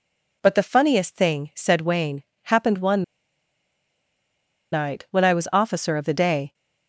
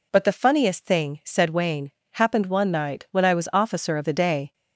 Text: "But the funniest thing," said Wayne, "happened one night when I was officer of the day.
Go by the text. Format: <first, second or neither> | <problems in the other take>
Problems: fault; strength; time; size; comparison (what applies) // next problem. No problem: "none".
second | pauses between "one" and "night"; strong; at 3.0 s; 1.7 s long